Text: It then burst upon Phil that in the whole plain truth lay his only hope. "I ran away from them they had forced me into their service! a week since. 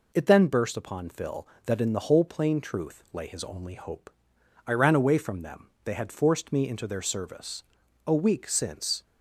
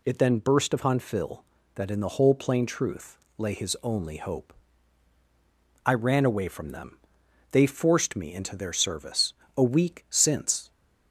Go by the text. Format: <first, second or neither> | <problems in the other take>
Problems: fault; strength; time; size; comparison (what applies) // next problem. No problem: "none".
first | pauses between "truth" and "lay"; slight; at 3.1 s; 0.20 s long // pauses between "them" and "they"; noticeable; at 6.9 s; 0.54 s long; slight in the first // skips "had"; at 7.6 s